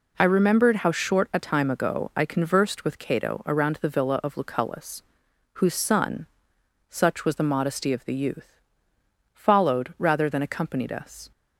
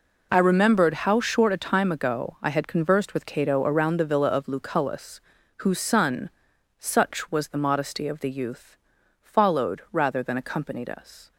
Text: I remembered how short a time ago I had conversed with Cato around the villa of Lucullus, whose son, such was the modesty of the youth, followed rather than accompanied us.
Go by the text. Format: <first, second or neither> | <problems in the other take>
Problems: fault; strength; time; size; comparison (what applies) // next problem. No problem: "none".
second | skips "had"; at 2.2 s